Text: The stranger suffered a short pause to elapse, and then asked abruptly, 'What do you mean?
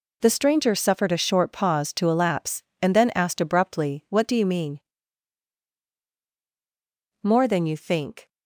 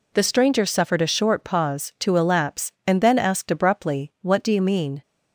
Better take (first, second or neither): second